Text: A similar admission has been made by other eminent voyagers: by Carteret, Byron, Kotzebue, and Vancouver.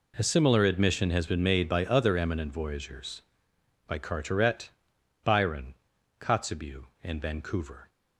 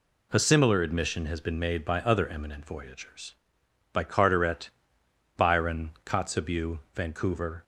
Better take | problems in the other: first | skips "and"; at 6.8 s

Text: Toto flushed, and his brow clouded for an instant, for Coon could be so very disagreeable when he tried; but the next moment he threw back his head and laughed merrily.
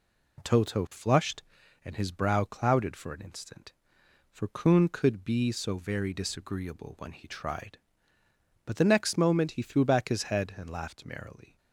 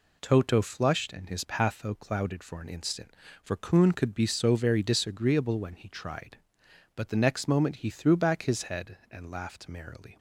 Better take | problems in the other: first | says "patho" for "brow"; at 1.4 s

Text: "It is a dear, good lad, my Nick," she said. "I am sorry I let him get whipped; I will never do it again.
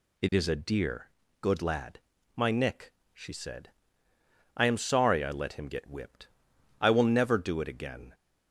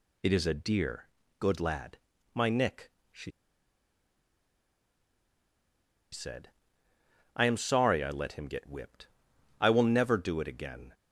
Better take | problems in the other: first | pauses between "she" and "said"; strong; at 3.3 s; 2.8 s long

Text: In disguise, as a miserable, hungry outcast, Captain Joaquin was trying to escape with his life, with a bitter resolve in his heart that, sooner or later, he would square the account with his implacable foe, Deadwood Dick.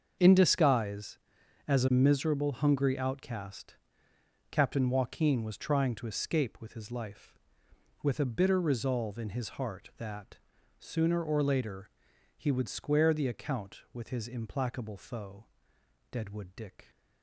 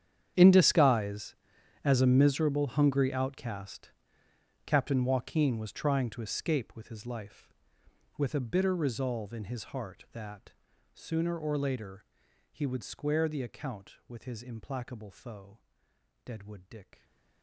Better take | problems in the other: first | gets quieter; strong; throughout; 19 dB // starts louder than the rest; strong; until 1.8 s; 9 dB; also in the first

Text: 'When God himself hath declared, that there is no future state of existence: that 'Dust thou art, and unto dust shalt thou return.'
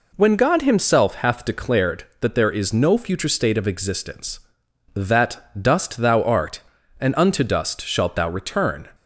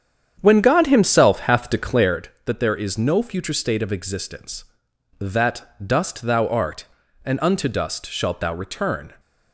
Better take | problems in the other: first | starts louder than the rest; strong; until 2.2 s; 8.5 dB // pauses between "that" and "Dust"; slight; at 5.6 s; 0.18 s long; slight in the first

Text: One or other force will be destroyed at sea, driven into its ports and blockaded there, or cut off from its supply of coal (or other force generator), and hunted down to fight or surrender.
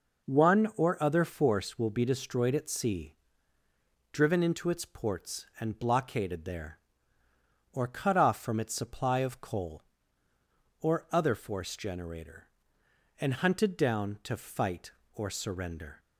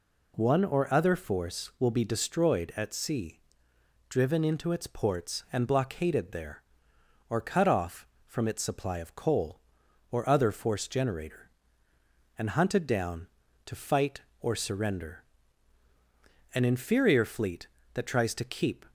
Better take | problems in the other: first | goes on to say "An inferior fleet that tries to keep"; strong; from 16.5 s on; 2.3 s long

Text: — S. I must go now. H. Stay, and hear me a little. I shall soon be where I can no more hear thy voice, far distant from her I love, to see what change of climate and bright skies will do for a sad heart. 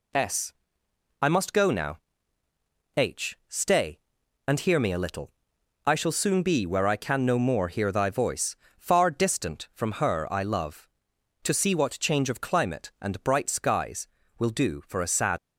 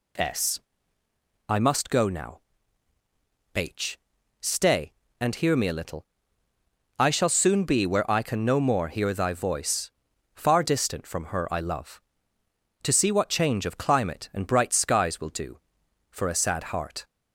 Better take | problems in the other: second | stops before "heart"; at 15.3 s

